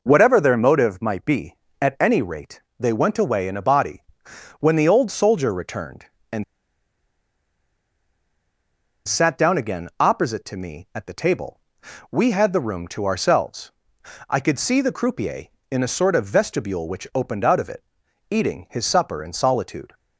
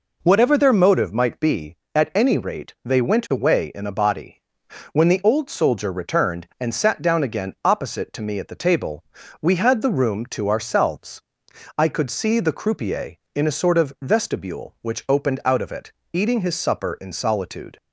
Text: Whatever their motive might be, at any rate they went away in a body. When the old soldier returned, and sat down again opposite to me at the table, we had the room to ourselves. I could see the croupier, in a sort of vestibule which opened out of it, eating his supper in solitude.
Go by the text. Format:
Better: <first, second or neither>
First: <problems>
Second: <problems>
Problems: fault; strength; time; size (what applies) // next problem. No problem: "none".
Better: second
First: pauses between "rate" and "they"; slight; at 2.6 s; 0.16 s long // pauses between "and" and "sat"; strong; at 6.4 s; 2.6 s long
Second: none